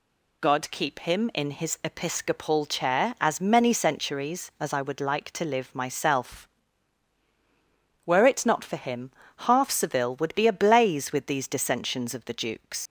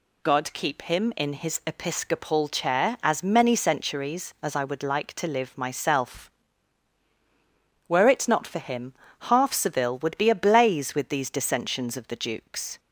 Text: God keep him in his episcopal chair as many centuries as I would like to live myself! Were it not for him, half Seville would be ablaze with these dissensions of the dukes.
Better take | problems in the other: second | leaves "dukes" unfinished; at 12.8 s; 110 ms

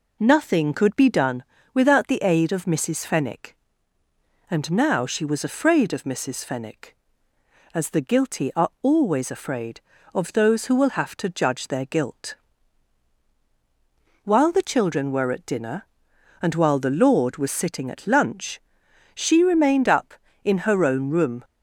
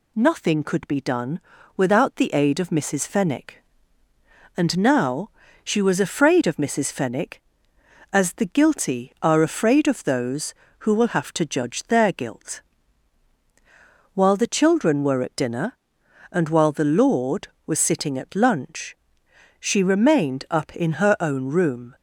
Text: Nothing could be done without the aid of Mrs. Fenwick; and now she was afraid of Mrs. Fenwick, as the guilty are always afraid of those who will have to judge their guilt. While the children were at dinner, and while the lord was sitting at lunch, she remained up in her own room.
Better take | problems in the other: first | pauses between "done" and "without"; slight; at 1.3 s; 0.36 s long; slight in the first // pauses between "now" and "she"; slight; at 5.2 s; 0.34 s long // skips "always"; at 9.4 s

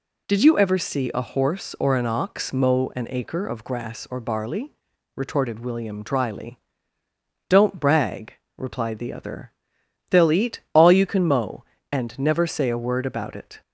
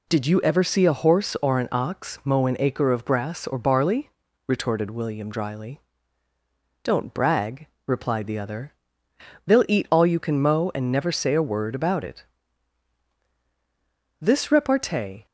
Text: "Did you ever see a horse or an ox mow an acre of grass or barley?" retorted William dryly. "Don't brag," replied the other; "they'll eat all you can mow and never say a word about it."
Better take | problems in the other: first | goes on to say "This repartee"; noticeable; from 14.2 s on; 1.0 s long

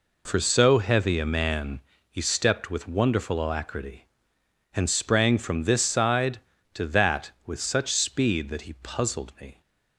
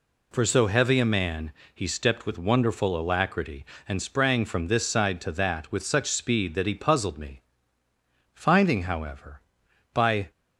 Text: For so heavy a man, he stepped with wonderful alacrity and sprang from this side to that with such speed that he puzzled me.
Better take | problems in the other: first | goes on to say "Finding however by"; strong; from 8.3 s on; 1.9 s long

